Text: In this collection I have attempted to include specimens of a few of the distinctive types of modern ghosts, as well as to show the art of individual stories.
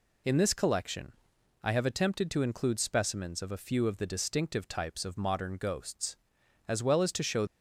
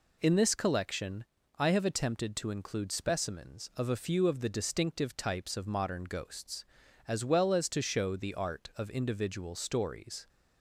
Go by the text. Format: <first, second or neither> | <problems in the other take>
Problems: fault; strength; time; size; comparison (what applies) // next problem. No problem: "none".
second | pauses between "collection" and "I"; noticeable; at 1.1 s; 0.50 s long; slight in the second // stops before "the art of individual stories"; at 7.4 s